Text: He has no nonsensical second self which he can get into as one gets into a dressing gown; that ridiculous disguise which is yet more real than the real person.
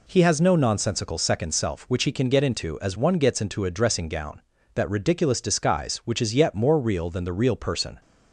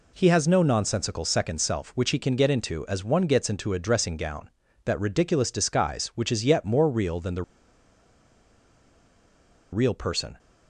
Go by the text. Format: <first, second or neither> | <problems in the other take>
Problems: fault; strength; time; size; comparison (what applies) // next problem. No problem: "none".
first | pauses between "the" and "real"; strong; at 7.4 s; 2.3 s long